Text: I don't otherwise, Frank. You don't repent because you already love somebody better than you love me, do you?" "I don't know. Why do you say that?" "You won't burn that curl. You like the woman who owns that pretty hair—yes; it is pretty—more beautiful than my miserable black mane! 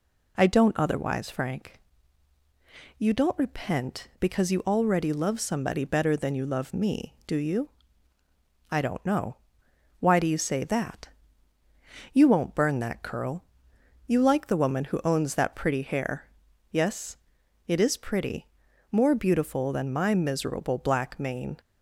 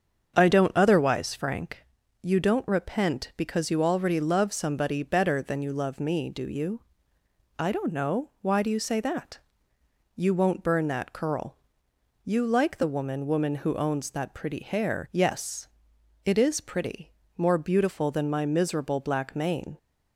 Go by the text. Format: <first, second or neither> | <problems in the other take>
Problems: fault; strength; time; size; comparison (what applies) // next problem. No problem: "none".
first | starts louder than the rest; until 1.3 s; 7 dB // says "woman" twice; at 13.2 s